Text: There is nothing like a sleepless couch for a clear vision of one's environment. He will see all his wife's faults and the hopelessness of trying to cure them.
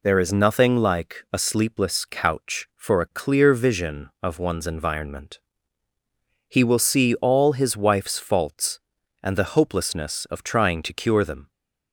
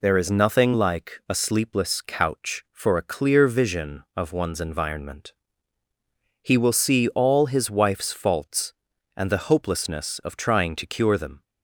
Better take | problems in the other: neither | none

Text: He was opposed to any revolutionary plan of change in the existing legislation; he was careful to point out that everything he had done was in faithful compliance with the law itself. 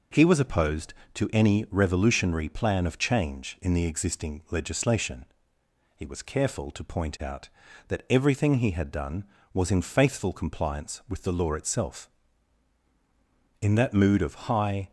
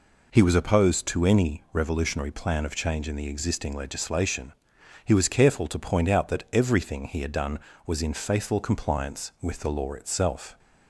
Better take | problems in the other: second | goes on to say "In that mood of high"; noticeable; from 13.6 s on; 1.3 s long

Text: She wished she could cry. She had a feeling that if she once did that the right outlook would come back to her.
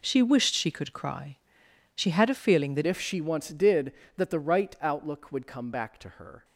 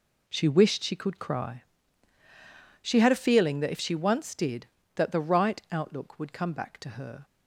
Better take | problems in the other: second | changes voice at "if"; from 2.8 s on; 3.6 s long

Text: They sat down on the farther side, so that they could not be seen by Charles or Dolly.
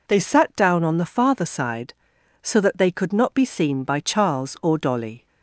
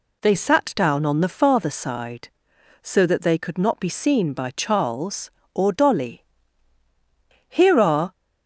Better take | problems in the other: first | goes on to say "Here are"; noticeable; from 7.4 s on; 0.64 s long

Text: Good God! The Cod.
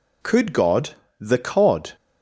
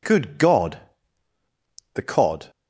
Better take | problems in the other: second | says "Could" for "Good"; at 0.2 s

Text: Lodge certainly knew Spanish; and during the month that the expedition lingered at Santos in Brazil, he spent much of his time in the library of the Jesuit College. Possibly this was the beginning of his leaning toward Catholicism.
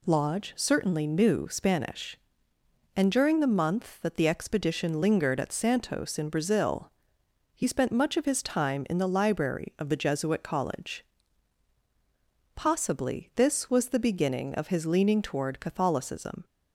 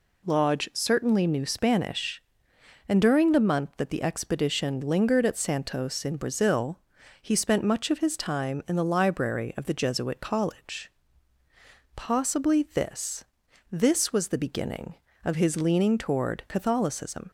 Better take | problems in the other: first | says "this" twice; at 13.7 s

